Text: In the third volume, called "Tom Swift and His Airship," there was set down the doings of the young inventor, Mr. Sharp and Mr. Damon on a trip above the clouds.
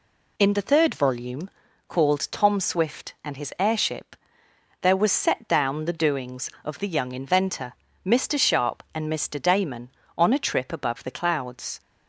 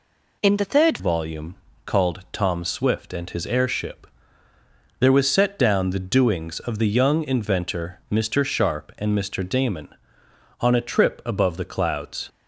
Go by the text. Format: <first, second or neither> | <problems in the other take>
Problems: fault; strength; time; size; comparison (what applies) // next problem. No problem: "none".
first | changes voice at "volume"; from 0.9 s on; 11.3 s long